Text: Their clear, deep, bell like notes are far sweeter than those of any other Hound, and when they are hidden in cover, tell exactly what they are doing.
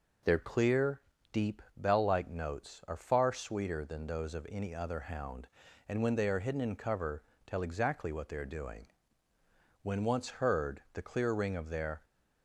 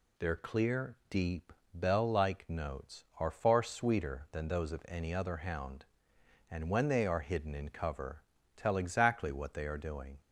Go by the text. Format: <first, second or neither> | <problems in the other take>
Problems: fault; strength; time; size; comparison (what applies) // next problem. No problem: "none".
second | goes on to say "When once heard the clear ring of their"; strong; from 9.8 s on; 2.2 s long